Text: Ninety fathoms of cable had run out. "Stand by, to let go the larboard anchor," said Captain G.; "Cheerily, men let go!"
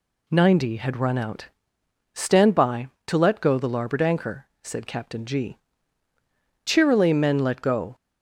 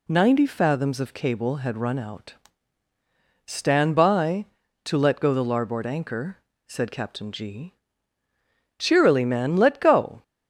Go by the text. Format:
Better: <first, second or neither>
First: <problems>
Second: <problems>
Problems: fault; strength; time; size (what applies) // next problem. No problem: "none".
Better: second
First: skips "fathoms of cable"; at 0.7 s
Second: none